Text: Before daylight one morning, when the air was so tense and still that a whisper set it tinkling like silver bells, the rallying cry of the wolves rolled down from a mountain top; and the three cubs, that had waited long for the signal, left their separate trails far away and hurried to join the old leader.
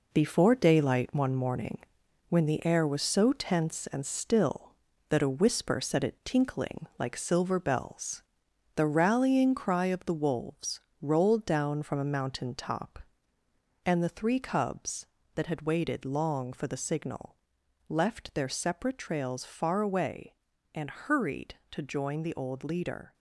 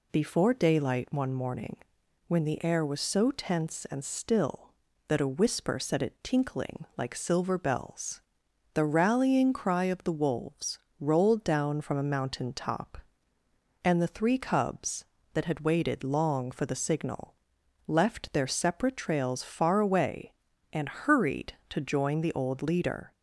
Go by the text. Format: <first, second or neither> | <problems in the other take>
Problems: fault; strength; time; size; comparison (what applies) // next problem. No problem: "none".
second | gets quieter; throughout; 7 dB // pauses between "wolves" and "rolled"; slight; at 10.8 s; 0.20 s long; slight in the second